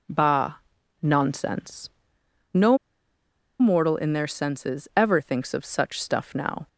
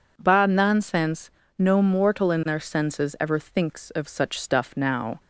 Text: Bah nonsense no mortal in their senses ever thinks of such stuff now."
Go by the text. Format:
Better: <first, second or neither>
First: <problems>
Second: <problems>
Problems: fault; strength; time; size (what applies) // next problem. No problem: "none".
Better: second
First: pauses between "Bah" and "nonsense"; noticeable; at 0.5 s; 0.46 s long // pauses between "nonsense" and "no"; noticeable; at 1.8 s; 0.64 s long // pauses between "no" and "mortal"; noticeable; at 2.7 s; 0.82 s long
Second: pauses between "nonsense" and "no"; slight; at 1.2 s; 0.28 s long